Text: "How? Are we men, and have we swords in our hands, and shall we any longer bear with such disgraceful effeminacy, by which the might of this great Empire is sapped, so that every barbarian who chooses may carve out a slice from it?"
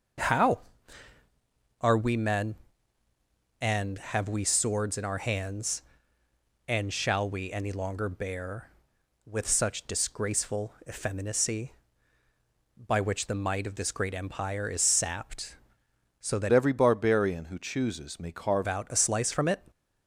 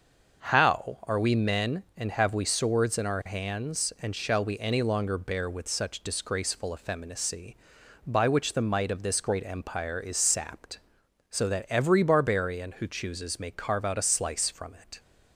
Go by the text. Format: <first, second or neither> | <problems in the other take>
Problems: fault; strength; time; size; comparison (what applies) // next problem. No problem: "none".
second | starts louder than the rest; until 2.4 s; 6.5 dB; also in the second // pauses between "disgraceful" and "effeminacy"; slight; at 10.7 s; 0.16 s long // changes voice from "every" to "carve"; from 16.5 to 18.6 s; 2.1 s long